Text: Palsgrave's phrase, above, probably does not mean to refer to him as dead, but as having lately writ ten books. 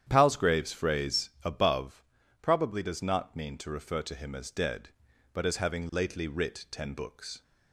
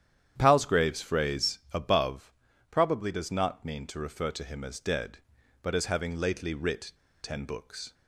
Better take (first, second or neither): first